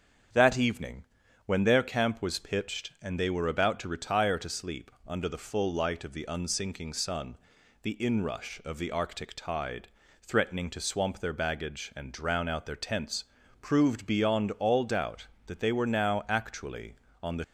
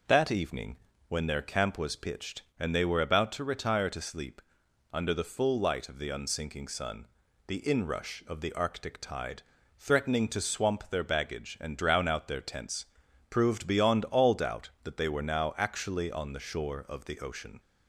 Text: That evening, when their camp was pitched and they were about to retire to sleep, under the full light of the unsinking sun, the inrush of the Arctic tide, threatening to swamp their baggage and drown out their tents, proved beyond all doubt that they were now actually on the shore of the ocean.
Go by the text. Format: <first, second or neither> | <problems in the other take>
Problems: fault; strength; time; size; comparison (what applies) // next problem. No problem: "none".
second | starts louder than the rest; strong; until 1.7 s; 7.5 dB // stops before "shore of the ocean"; at 17.4 s